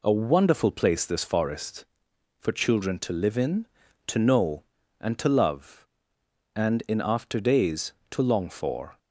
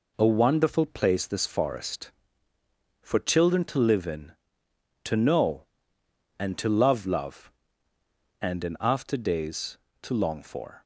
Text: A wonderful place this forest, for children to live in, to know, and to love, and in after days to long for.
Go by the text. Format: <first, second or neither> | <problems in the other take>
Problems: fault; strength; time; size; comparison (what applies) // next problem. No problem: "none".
first | says "love" twice; at 7.0 s